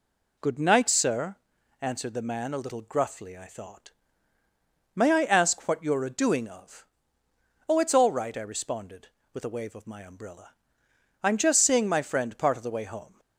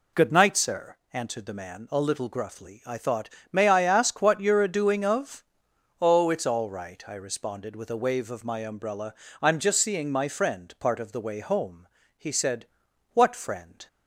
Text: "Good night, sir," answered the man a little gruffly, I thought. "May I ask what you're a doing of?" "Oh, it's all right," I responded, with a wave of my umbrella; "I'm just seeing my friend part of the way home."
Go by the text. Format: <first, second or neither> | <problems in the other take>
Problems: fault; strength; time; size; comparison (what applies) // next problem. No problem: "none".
first | goes on to say "He said What friend"; strong; from 12.1 s on; 1.6 s long